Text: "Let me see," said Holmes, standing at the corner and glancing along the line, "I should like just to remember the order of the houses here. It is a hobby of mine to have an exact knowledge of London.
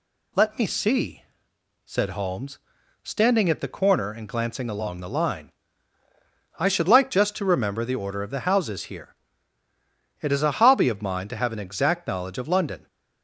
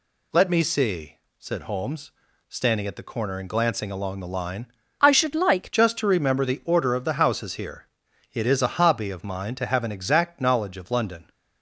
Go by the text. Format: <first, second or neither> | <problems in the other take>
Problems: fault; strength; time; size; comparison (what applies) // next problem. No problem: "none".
first | changes voice from "I" to "like"; from 4.9 to 5.6 s; 0.7 s long